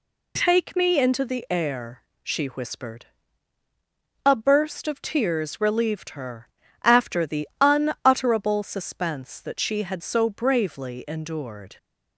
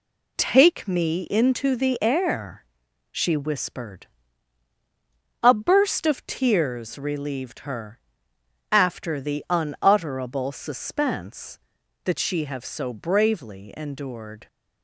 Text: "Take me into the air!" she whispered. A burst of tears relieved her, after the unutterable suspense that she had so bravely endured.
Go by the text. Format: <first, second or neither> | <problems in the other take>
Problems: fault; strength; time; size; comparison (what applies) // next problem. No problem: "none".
first | says "have" for "had"; at 12.4 s